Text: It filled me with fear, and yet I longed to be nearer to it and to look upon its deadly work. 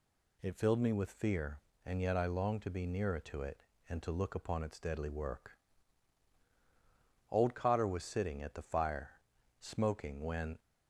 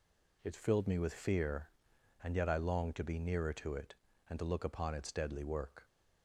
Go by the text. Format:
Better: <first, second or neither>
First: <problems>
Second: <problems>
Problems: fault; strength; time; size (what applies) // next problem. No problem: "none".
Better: second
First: goes on to say "Old Cotter was sitting at the fire smoking when"; strong; from 7.2 s on; 3.3 s long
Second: none